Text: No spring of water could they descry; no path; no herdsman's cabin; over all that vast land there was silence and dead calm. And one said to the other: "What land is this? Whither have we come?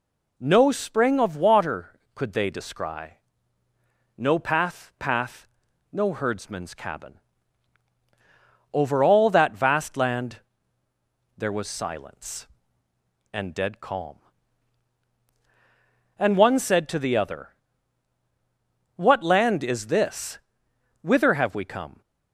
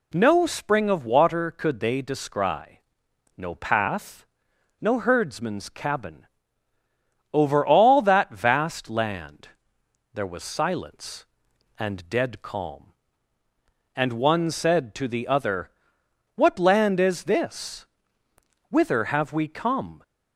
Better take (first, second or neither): second